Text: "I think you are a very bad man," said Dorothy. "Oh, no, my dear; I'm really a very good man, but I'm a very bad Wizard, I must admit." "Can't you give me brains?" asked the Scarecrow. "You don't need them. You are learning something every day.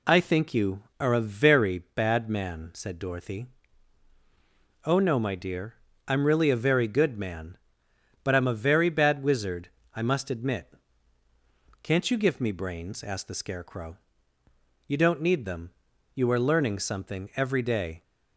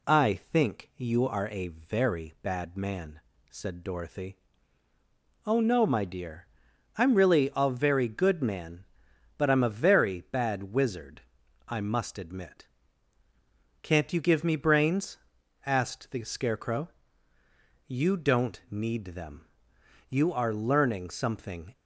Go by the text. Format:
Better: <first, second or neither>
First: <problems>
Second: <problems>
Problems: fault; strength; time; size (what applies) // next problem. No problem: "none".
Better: first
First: none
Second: stops before "every day"; at 21.7 s